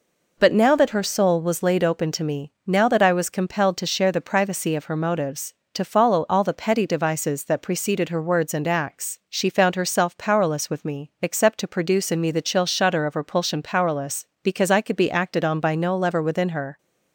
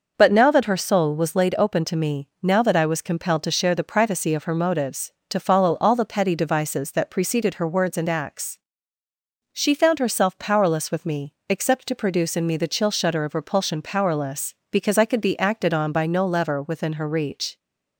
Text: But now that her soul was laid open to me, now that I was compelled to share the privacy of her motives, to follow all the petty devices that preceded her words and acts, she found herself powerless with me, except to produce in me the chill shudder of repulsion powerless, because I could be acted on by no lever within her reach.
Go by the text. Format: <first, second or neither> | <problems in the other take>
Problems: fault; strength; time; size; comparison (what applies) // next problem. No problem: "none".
second | stops before "reach"; at 16.7 s